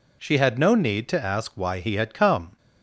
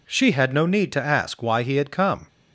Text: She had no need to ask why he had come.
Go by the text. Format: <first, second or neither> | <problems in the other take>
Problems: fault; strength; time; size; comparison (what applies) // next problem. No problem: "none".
neither | none